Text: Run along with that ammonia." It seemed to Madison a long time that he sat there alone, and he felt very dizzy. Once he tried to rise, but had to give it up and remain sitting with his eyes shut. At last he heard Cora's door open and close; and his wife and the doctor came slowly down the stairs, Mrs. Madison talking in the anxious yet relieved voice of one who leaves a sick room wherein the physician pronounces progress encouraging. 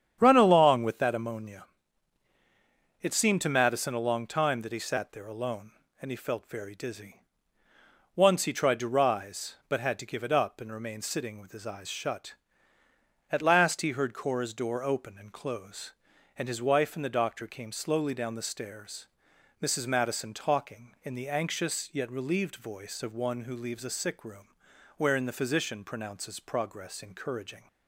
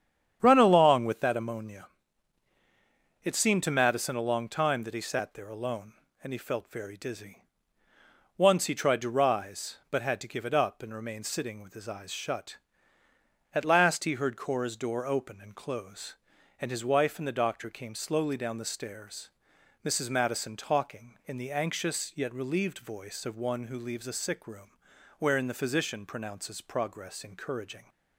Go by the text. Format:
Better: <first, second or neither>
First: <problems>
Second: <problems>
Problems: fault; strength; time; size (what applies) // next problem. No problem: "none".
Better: neither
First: starts louder than the rest; strong; until 1.2 s; 9 dB // pauses between "room" and "wherein"; noticeable; at 24.4 s; 0.50 s long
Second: starts louder than the rest; strong; until 1.4 s; 9 dB // pauses between "room" and "wherein"; noticeable; at 24.6 s; 0.48 s long